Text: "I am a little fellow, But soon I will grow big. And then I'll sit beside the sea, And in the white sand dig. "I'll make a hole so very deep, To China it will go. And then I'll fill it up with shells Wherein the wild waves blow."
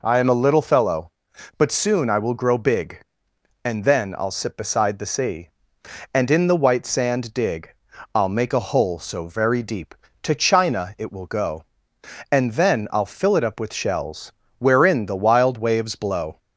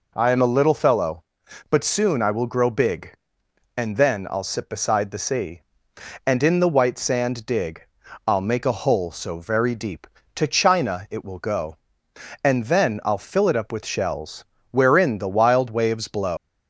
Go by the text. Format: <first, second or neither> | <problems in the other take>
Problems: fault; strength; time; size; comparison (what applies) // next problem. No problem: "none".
first | pauses between "shells" and "Wherein"; slight; at 14.4 s; 0.24 s long; slight in the first // leaves "blow" unfinished; at 16.3 s; 135 ms